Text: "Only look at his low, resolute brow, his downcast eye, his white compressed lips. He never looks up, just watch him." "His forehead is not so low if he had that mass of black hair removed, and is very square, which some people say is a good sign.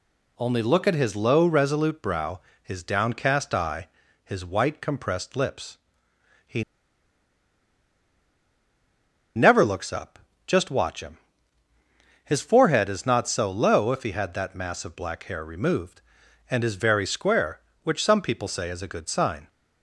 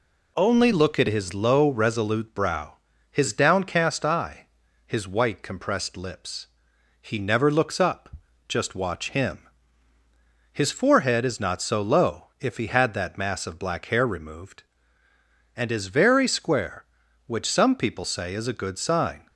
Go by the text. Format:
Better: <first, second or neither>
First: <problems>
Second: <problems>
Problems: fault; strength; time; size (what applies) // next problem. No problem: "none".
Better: second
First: pauses between "He" and "never"; strong; at 6.6 s; 2.7 s long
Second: none